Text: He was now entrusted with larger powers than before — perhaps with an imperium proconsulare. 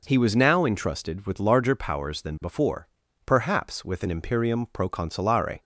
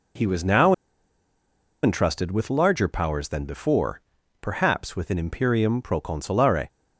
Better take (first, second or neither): first